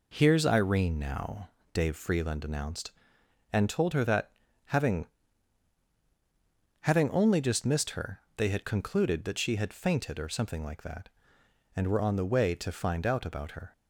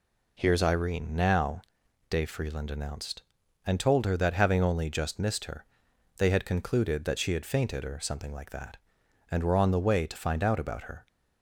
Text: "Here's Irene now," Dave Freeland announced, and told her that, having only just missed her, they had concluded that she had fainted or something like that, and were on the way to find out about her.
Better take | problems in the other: second | says "having" twice; at 6.8 s

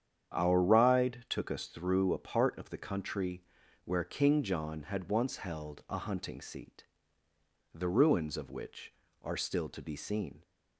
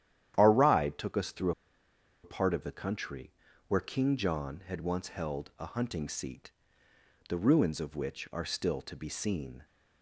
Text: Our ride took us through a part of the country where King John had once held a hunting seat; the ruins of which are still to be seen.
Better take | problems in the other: first | starts louder than the rest; strong; until 1.3 s; 11 dB; strong in the first // pauses between "through" and "a"; noticeable; at 1.5 s; 0.72 s long // pauses between "country" and "where"; slight; at 3.3 s; 0.36 s long; also in the first

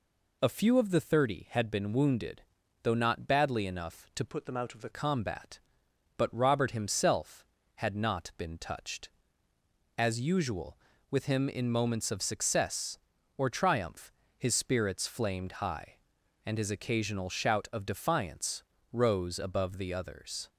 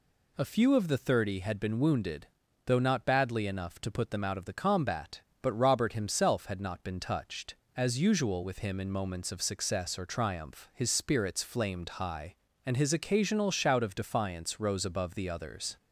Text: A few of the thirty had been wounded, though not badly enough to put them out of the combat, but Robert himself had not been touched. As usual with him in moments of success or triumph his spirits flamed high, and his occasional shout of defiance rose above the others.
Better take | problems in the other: second | changes voice from "put" to "the"; from 4.2 to 4.8 s; 0.6 s long // pauses between "triumph" and "his"; slight; at 14.1 s; 0.26 s long // pauses between "defiance" and "rose"; slight; at 18.6 s; 0.30 s long

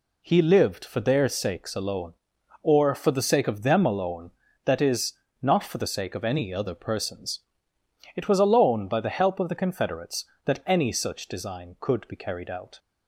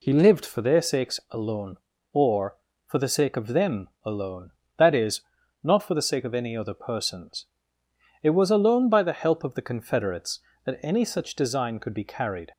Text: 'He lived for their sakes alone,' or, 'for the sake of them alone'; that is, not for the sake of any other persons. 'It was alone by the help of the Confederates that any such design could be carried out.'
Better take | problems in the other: first | pauses between "them" and "alone"; slight; at 3.8 s; 0.16 s long // stops before "out"; at 12.5 s

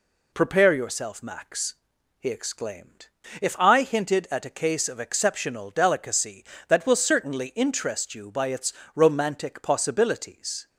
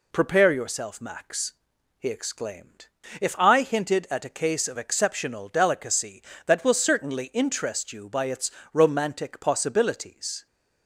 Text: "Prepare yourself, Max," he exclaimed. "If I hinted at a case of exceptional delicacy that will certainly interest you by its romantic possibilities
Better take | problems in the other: neither | pauses between "its" and "romantic"; slight; the same in both

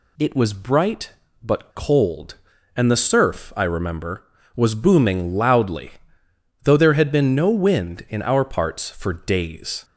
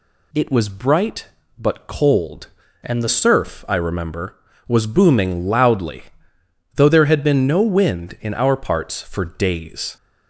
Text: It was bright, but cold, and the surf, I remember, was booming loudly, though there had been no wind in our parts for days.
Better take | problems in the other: first | changes voice from "and" to "the"; from 2.8 to 3.0 s; 0.2 s long

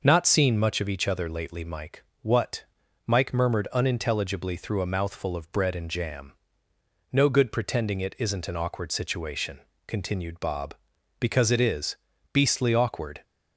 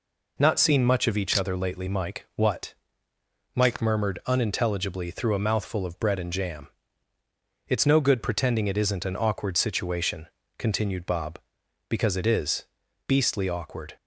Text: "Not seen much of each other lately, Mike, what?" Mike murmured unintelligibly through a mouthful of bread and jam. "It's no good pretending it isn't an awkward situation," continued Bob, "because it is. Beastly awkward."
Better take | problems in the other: second | skips "It's"; at 6.7 s

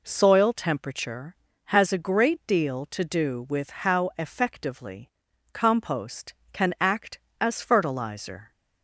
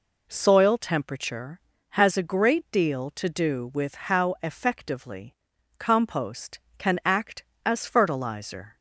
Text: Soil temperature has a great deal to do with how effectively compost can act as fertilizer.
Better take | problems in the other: neither | pauses between "effectively" and "compost"; the same in both

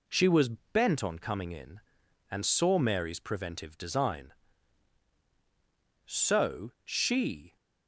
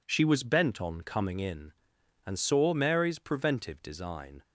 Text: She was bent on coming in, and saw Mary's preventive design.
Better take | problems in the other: second | goes on to say "So she"; from 6.0 s on; 1.5 s long

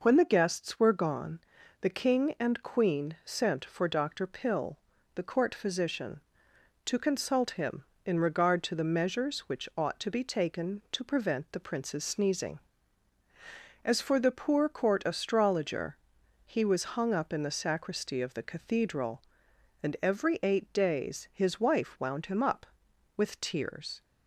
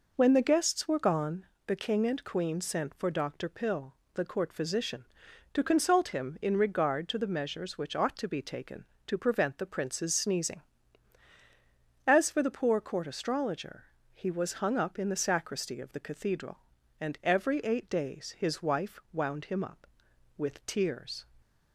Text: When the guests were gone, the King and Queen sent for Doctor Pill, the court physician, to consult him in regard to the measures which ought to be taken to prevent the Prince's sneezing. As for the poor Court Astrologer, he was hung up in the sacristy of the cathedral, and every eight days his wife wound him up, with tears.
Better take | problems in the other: neither | none

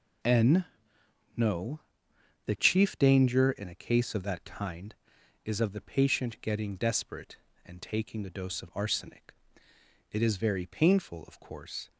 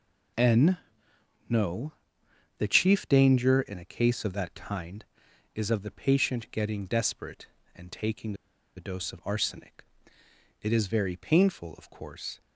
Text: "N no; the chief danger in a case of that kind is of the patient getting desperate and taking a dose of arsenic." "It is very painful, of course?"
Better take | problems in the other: first | pauses between "N" and "no"; noticeable; at 0.7 s; 0.70 s long; noticeable in the first // pauses between "taking" and "a"; at 8.3 s; 0.42 s long

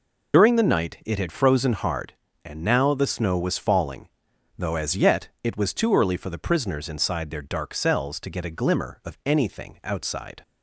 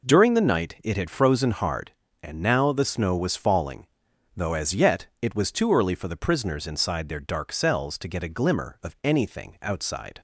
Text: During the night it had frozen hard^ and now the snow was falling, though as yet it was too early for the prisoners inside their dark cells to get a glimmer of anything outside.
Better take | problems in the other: second | loses the start of "During"; at 0.3 s; 90 ms // pauses between "yet" and "it"; slight; at 5.2 s; 0.16 s long; slight in the second

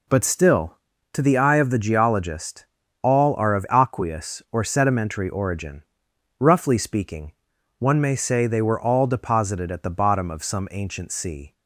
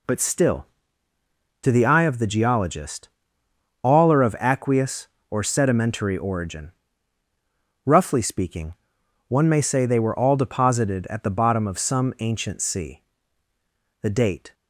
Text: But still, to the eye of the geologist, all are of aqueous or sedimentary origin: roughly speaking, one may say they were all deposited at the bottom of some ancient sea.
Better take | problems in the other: first | goes on to say "The date"; from 14.0 s on; 0.52 s long

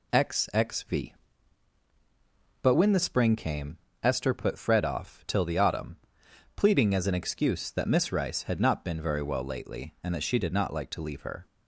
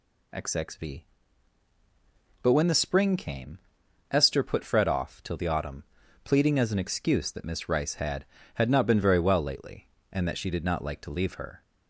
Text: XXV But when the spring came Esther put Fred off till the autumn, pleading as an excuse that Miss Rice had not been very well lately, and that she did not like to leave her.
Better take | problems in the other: first | pauses between "came" and "Esther"; noticeable; at 3.5 s; 0.52 s long; slight in the first // says "had" twice; at 8.5 s

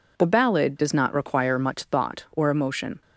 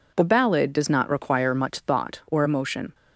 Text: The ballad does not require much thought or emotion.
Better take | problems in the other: neither | none

